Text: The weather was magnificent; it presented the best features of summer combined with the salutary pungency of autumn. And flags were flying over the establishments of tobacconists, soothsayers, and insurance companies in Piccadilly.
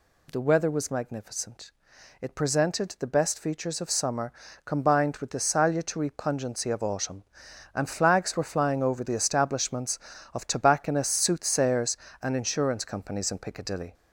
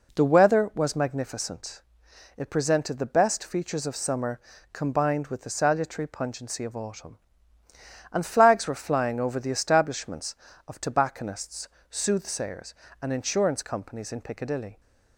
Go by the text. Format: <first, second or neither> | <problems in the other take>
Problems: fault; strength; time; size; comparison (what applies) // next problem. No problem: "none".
second | gets louder; slight; throughout; 2.5 dB // pauses between "summer" and "combined"; slight; at 4.3 s; 0.32 s long; slight in the second